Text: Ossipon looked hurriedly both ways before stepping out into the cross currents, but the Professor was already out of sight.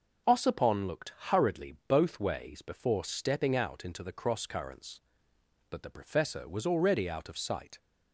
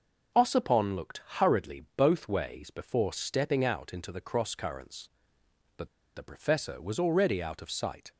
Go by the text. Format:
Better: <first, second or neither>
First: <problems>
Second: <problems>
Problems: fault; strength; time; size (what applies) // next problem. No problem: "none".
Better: first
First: starts louder than the rest; strong; until 1.4 s; 7 dB // pauses between "looked" and "hurriedly"; slight; at 1.1 s; 0.16 s long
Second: starts louder than the rest; strong; until 1.5 s; 7 dB // pauses between "looked" and "hurriedly"; slight; at 1.2 s; 0.16 s long // pauses between "but" and "the"; slight; at 5.8 s; 0.28 s long